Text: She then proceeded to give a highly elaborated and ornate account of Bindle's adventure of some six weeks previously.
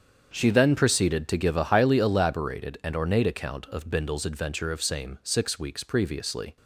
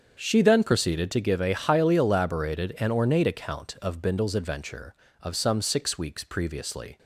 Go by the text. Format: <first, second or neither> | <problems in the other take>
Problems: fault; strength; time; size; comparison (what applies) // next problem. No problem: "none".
second | starts louder than the rest; strong; until 1.3 s; 7.5 dB; strong in the second // says "same" for "some"; at 4.8 s